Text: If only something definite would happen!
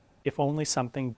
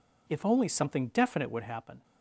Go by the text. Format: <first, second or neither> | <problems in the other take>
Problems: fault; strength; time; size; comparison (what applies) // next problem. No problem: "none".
second | stops before "definite would happen"; at 1.1 s